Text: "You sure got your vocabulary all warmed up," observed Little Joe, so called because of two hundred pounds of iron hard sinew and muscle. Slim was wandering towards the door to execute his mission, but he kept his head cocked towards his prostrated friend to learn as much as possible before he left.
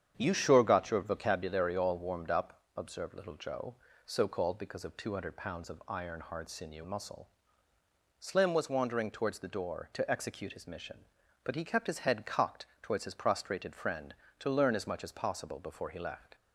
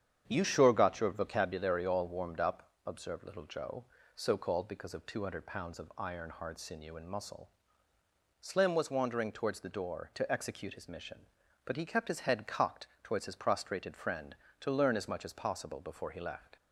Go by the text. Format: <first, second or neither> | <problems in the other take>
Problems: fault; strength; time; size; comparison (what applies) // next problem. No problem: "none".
second | starts louder than the rest; strong; until 1.1 s; 8.5 dB; strong in the second // skips "and"; at 6.8 s // pauses between "cocked" and "towards"; slight; at 12.6 s; 0.16 s long; slight in the second